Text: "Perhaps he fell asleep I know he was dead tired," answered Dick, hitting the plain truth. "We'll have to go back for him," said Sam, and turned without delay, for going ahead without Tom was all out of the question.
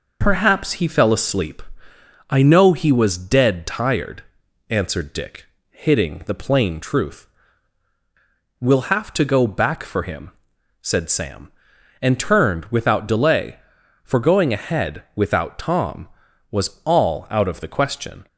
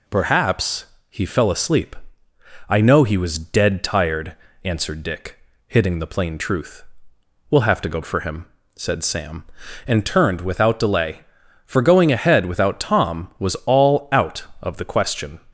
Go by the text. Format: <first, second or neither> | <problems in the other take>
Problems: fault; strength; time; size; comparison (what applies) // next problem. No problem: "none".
first | pauses between "Perhaps" and "he"; slight; at 0.8 s; 0.24 s long // pauses between "asleep" and "I"; noticeable; at 1.9 s; 0.74 s long; noticeable in the first // skips "back"; at 8.0 s